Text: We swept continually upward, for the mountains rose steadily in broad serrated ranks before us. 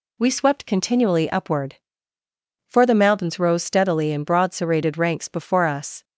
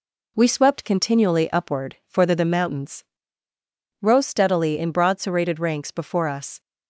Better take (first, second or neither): first